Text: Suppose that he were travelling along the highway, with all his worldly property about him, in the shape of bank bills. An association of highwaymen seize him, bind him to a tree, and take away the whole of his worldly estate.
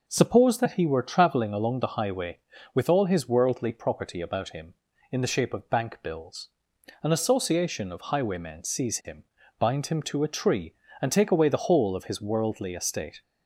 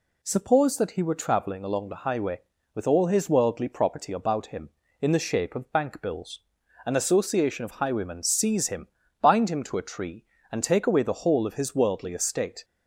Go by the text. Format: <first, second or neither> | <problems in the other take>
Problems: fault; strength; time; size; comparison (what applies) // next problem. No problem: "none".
neither | none